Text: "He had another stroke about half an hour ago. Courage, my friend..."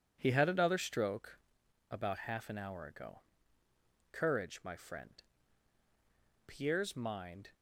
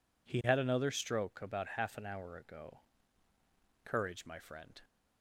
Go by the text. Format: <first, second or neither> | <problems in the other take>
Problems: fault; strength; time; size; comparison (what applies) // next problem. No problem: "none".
second | pauses between "stroke" and "about"; noticeable; at 1.3 s; 0.50 s long // goes on to say "Pierre's mind"; noticeable; from 6.4 s on; 1.0 s long